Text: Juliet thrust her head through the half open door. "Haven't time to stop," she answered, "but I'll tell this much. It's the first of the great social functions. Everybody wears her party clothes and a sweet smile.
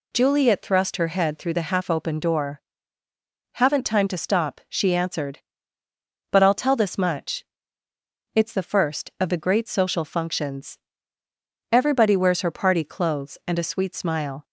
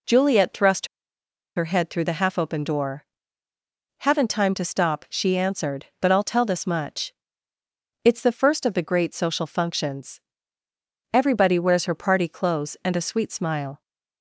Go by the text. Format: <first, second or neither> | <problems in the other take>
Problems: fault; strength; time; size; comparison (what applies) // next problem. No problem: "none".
first | pauses between "thrust" and "her"; noticeable; at 0.8 s; 0.69 s long